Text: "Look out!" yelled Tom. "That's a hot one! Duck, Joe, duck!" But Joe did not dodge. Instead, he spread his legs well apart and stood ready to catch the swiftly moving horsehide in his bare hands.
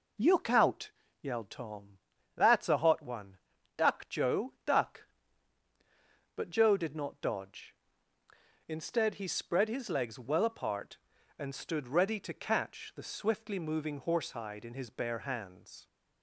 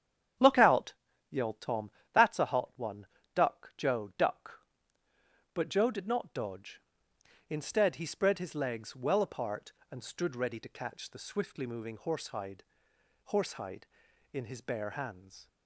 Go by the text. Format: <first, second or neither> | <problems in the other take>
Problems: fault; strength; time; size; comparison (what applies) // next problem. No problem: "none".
first | starts louder than the rest; strong; until 1.7 s; 9 dB // says "horsehide" twice; at 13.2 s